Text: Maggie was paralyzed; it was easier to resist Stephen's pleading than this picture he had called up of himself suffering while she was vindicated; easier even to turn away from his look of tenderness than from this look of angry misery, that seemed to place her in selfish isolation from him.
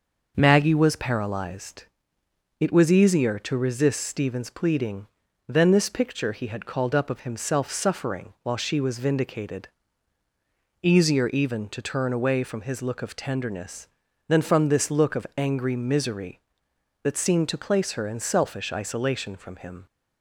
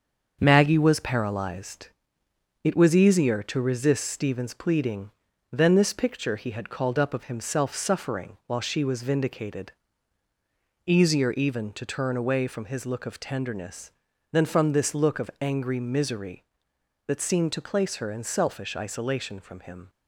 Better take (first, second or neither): first